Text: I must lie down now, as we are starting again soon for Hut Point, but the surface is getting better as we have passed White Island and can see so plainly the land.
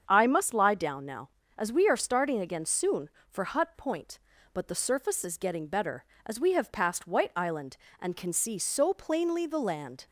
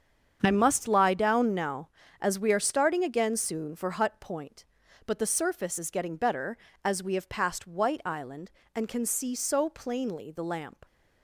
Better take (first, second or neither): first